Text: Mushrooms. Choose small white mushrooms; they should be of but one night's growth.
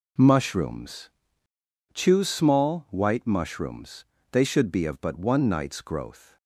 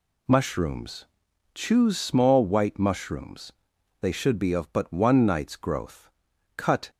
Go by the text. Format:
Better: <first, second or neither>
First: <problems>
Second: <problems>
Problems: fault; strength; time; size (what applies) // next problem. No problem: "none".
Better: first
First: none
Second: goes on to say "Cut"; slight; from 6.5 s on; 0.34 s long